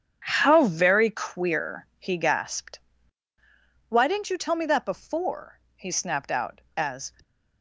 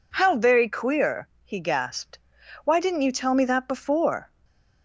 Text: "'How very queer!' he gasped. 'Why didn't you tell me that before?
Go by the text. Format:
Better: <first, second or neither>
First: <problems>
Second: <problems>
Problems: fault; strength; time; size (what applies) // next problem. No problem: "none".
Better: second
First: starts louder than the rest; strong; until 1.2 s; 8 dB // goes on to say "he snapped out as"; from 5.7 s on; 1.3 s long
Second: none